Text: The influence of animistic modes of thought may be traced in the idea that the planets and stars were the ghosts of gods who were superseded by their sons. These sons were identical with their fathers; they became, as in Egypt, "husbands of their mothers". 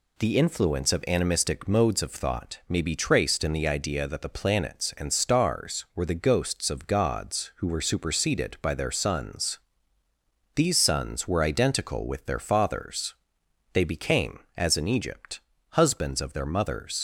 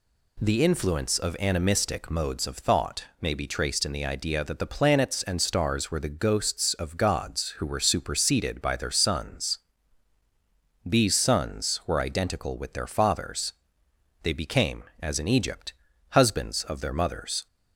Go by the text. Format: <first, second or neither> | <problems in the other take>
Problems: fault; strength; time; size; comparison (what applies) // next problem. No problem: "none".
second | leaves "mothers" unfinished; at 16.9 s; 65 ms